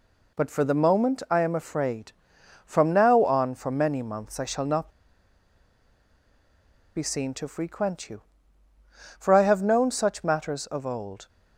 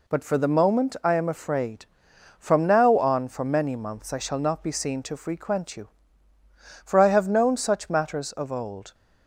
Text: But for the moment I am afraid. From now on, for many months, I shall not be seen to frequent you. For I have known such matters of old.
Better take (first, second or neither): second